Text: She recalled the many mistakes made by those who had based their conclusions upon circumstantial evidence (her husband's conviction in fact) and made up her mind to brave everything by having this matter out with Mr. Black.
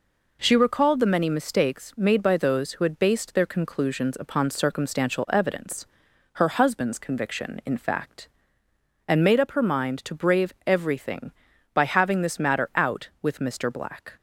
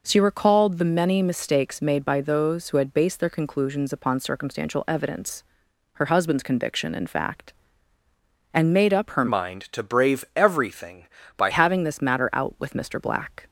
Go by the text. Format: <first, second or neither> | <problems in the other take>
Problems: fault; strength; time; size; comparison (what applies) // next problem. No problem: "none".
first | changes voice from "mind" to "by"; from 9.2 to 11.5 s; 2.3 s long